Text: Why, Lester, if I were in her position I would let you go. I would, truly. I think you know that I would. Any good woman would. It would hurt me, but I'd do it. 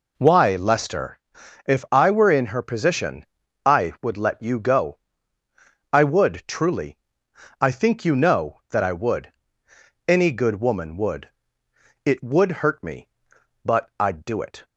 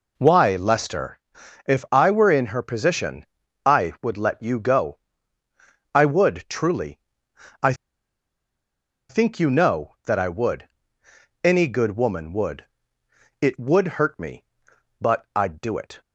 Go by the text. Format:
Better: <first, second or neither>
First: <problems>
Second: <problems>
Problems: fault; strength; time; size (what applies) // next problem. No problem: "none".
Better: first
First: pauses between "position" and "I"; at 3.2 s; 0.40 s long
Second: pauses between "position" and "I"; at 3.2 s; 0.40 s long // pauses between "I" and "think"; strong; at 7.7 s; 1.3 s long